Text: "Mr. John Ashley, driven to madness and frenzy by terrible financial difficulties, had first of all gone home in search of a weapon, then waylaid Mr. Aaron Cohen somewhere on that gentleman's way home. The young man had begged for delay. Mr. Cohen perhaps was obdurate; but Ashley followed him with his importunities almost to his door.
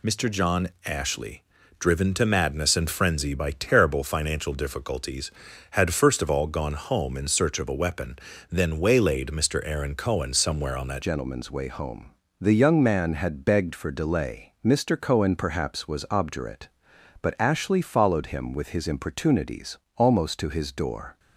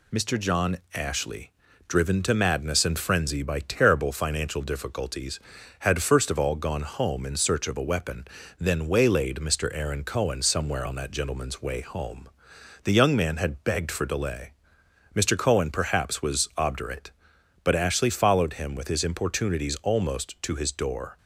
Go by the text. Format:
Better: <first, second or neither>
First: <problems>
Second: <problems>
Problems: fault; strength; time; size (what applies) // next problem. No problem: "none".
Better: second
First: pauses between "John" and "Ashley"; slight; at 0.6 s; 0.16 s long // changes voice at "gentleman's"; from 11.0 s on; 10.1 s long // pauses between "importunities" and "almost"; slight; at 19.7 s; 0.18 s long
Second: pauses between "John" and "Ashley"; slight; at 0.7 s; 0.16 s long